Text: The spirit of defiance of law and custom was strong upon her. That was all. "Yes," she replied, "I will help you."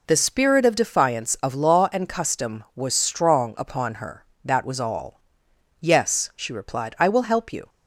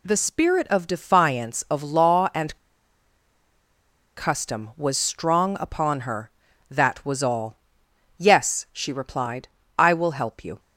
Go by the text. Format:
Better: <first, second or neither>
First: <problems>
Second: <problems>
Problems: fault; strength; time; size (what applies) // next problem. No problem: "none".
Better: first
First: none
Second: pauses between "and" and "custom"; strong; at 2.5 s; 1.6 s long